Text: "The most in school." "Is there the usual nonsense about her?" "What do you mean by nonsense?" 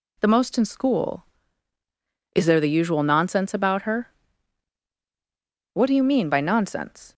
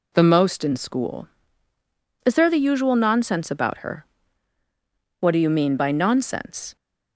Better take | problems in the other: neither | none

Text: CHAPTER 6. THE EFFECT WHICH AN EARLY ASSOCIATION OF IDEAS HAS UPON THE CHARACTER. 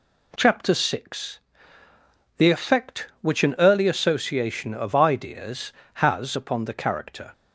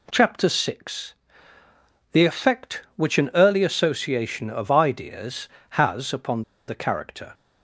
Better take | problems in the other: first | pauses between "UPON" and "THE"; slight; at 6.4 s; 0.25 s long

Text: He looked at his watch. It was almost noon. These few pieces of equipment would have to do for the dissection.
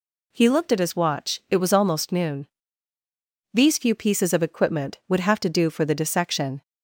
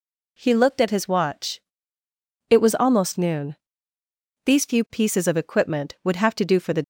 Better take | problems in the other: first | stops before "dissection"; at 6.8 s

